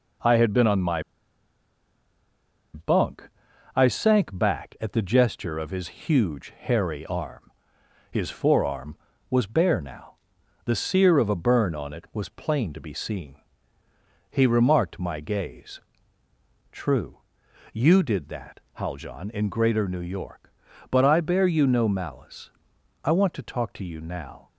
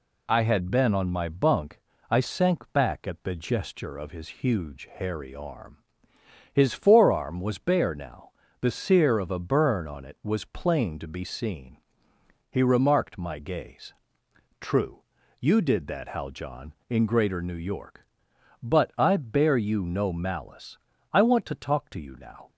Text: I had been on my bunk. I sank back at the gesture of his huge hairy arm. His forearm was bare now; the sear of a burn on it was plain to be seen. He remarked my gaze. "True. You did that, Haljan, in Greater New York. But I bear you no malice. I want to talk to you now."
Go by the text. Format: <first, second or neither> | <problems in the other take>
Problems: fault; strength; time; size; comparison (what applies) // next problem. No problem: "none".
second | pauses between "my" and "bunk"; strong; at 1.0 s; 1.7 s long